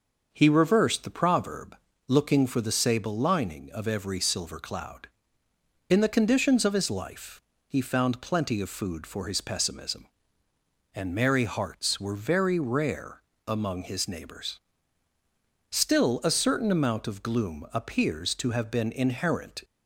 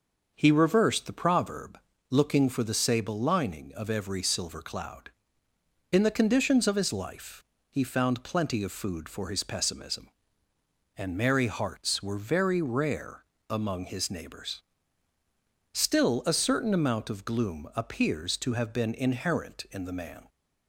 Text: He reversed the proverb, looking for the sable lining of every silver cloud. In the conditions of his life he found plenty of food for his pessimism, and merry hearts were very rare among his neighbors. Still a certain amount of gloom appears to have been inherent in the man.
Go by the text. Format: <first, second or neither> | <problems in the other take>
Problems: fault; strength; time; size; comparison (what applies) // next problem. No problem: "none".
second | pauses between "life" and "he"; slight; at 7.3 s; 0.28 s long; slight in the second // pauses between "rare" and "among"; slight; at 13.2 s; 0.24 s long; slight in the second // stops before "in the man"; at 19.6 s